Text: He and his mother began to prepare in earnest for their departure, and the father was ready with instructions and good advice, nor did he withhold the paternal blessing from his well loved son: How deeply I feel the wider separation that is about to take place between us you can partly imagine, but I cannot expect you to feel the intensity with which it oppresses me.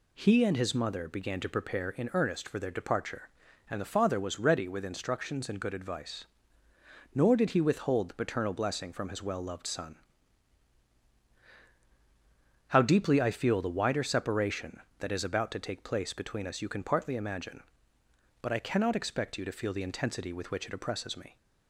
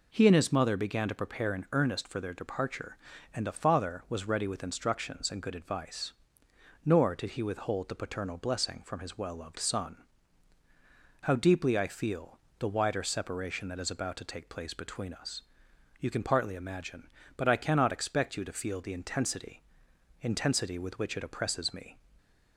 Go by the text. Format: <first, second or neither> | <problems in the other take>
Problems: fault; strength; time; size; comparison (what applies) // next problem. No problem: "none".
first | pauses between "feel" and "the"; slight; at 12.3 s; 0.20 s long // pauses between "us" and "you"; noticeable; at 15.4 s; 0.58 s long // says "intensity" twice; at 20.1 s